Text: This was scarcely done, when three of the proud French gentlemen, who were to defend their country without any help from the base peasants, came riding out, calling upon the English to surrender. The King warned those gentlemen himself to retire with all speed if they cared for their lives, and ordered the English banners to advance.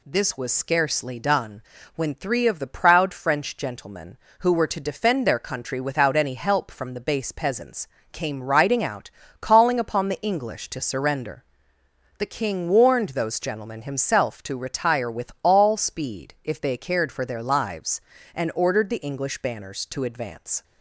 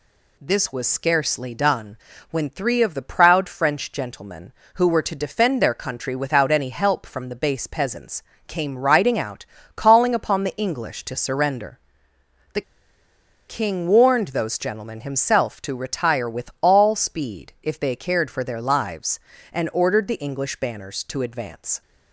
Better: first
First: none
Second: pauses between "The" and "King"; noticeable; at 12.6 s; 0.86 s long

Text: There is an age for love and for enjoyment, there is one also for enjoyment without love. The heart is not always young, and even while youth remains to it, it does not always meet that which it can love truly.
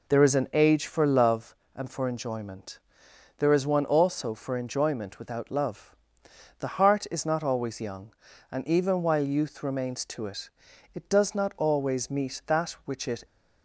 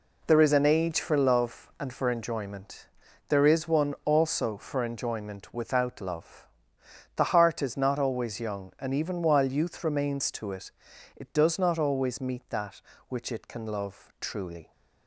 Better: second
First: stops before "can love truly"; at 13.2 s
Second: none

